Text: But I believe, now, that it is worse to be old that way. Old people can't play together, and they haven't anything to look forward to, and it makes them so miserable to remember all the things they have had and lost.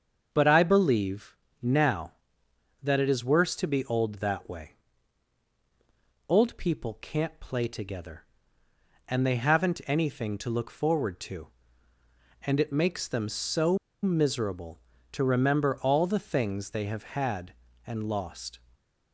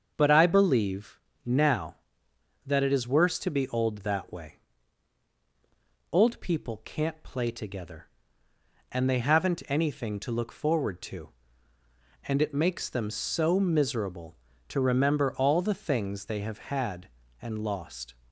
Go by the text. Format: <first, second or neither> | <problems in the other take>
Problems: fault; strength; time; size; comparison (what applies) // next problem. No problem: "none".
second | starts louder than the rest; until 1.3 s; 6.5 dB; also in the second // pauses between "so" and "miserable"; slight; at 13.7 s; 0.25 s long